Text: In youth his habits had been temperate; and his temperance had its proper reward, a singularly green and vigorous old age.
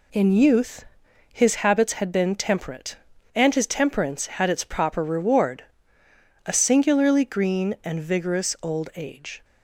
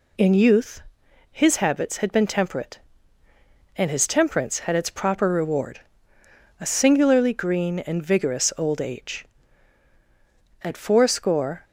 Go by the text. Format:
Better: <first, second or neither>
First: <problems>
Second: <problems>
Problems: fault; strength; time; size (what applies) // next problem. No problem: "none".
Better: first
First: pauses between "youth" and "his"; noticeable; at 0.8 s; 0.48 s long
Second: pauses between "youth" and "his"; noticeable; at 0.8 s; 0.48 s long // goes on to say "At fourscore"; noticeable; from 10.6 s on; 1.0 s long